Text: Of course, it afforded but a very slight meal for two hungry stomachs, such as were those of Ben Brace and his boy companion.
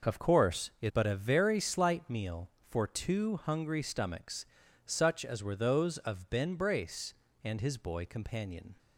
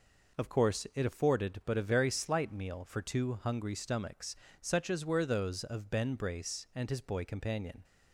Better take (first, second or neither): second